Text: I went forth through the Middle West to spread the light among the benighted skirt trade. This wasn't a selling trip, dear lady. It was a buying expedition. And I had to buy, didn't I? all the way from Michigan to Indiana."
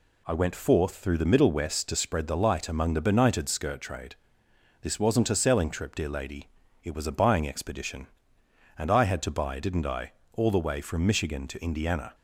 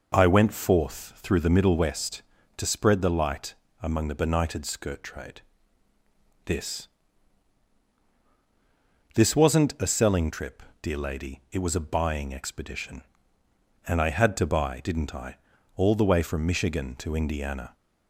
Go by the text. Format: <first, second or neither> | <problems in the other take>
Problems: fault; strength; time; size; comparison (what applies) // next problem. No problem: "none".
first | pauses between "light" and "among"; slight; at 3.5 s; 0.26 s long // says "This" twice; at 9.1 s